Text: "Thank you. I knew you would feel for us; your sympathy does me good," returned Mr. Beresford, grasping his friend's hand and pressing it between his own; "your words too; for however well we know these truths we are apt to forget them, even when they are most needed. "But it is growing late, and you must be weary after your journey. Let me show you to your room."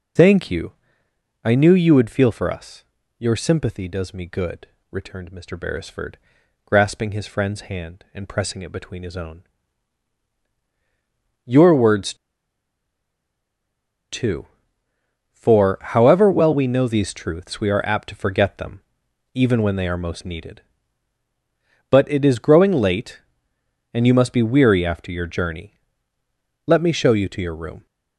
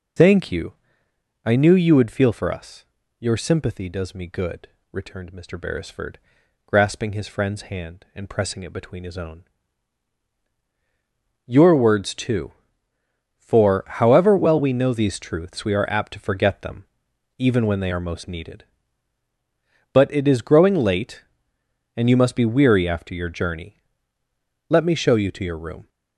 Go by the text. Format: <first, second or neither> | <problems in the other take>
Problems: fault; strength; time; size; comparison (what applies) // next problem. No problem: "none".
second | pauses between "words" and "too"; strong; at 12.1 s; 1.9 s long